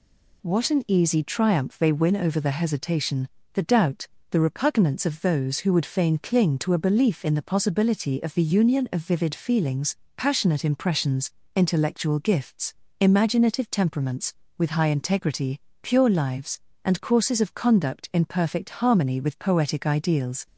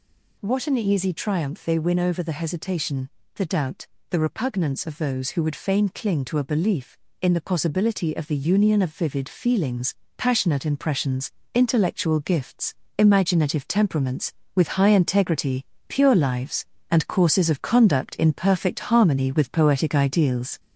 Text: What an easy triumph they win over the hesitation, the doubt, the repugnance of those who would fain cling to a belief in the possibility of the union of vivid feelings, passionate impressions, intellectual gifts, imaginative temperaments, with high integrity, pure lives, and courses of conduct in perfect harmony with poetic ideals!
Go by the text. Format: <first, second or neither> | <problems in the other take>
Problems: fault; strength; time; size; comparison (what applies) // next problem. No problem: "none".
first | gets louder; slight; throughout; 3.5 dB